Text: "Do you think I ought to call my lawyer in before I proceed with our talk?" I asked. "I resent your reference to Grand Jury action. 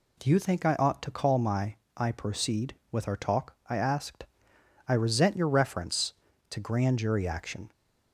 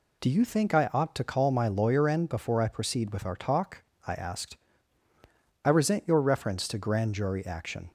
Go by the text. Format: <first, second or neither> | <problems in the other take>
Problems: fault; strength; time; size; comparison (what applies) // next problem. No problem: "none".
second | skips "lawyer in before"; at 1.8 s